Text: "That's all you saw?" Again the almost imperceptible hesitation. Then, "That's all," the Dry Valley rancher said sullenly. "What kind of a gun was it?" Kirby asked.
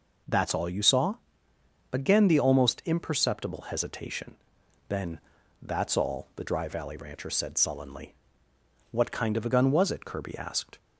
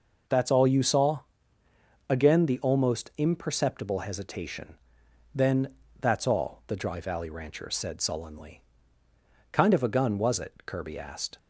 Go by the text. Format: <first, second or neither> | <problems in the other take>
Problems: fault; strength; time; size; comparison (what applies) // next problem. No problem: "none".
first | skips "What"; at 9.0 s